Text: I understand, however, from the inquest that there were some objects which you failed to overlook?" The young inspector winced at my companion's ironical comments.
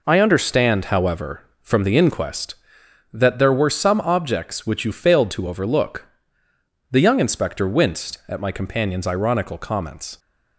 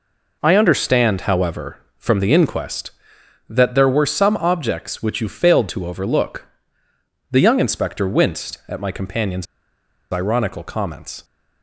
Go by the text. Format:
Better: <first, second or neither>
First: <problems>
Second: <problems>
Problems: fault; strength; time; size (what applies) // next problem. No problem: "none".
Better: first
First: none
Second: pauses between "companion's" and "ironical"; noticeable; at 9.4 s; 0.68 s long